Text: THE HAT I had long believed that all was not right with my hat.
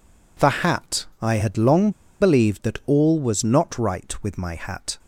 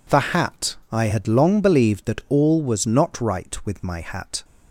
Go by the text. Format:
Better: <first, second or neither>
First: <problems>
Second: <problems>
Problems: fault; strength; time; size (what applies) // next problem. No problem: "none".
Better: second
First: pauses between "long" and "believed"; slight; at 1.8 s; 0.30 s long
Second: none